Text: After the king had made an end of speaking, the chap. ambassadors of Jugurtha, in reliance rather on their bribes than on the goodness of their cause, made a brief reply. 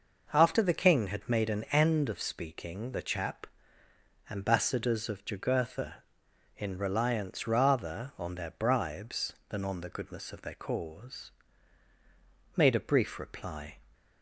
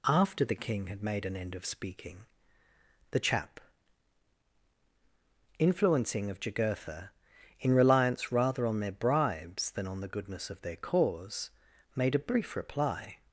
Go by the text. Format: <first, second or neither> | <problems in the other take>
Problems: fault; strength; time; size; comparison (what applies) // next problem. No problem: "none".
first | says "influencing" for "ambassadors"; at 5.5 s